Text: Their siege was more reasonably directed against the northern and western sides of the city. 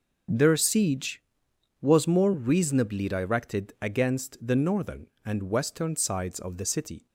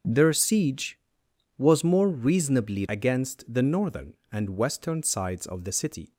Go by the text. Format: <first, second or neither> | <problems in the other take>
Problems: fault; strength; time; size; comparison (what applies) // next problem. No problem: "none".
first | skips "directed"; at 2.8 s